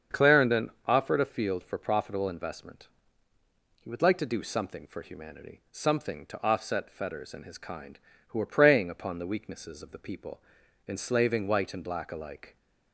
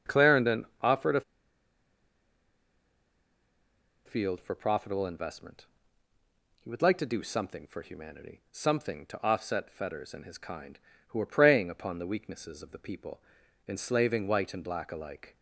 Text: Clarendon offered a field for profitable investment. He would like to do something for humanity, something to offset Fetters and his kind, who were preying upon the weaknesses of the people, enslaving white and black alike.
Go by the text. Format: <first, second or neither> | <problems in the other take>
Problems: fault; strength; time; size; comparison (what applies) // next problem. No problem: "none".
first | starts louder than the rest; strong; until 1.1 s; 7 dB; strong in the first // pauses between "a" and "field"; strong; at 1.2 s; 2.8 s long